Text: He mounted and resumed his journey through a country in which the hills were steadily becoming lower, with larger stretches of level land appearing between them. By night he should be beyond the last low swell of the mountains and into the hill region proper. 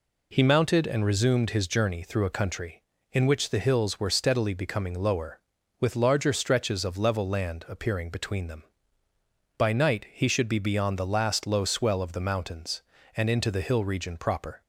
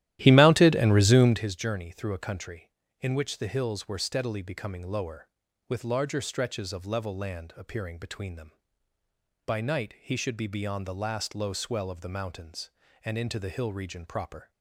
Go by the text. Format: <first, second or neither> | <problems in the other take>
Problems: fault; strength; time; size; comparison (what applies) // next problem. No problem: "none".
first | starts louder than the rest; strong; until 1.4 s; 13.5 dB